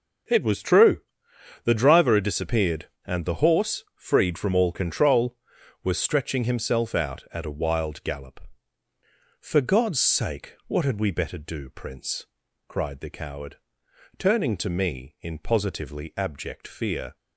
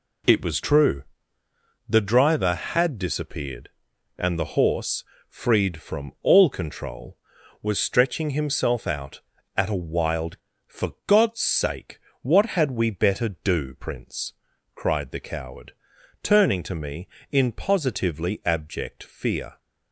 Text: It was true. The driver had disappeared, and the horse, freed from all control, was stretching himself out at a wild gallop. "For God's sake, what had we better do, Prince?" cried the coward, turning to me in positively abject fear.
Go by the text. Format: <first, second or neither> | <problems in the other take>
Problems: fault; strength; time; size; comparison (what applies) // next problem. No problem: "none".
first | skips "gallop"; at 10.5 s